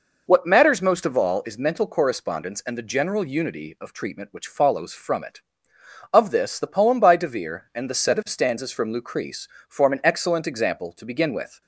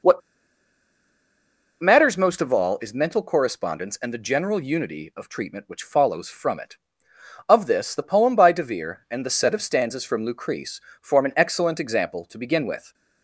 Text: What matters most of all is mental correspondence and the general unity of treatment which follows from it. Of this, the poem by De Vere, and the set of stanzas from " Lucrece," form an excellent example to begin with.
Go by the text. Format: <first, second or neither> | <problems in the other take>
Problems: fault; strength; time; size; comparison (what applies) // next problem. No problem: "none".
first | pauses between "What" and "matters"; strong; at 0.2 s; 1.6 s long